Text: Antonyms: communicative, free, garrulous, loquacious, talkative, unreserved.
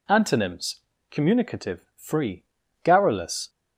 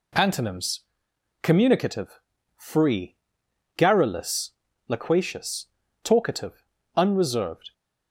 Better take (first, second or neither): second